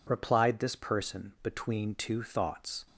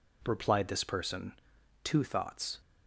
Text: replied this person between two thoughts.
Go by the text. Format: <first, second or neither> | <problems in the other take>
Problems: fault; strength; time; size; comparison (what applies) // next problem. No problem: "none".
first | skips "between"; at 1.5 s